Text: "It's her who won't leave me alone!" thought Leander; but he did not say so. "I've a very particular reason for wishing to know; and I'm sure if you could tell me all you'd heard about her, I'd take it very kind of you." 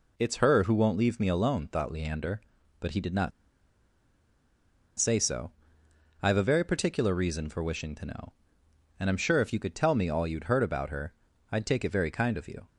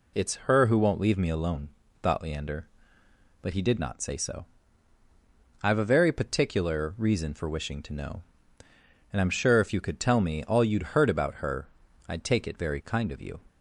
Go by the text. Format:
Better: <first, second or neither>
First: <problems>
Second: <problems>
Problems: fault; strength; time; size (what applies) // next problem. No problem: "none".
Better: second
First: pauses between "not" and "say"; strong; at 3.3 s; 1.6 s long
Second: none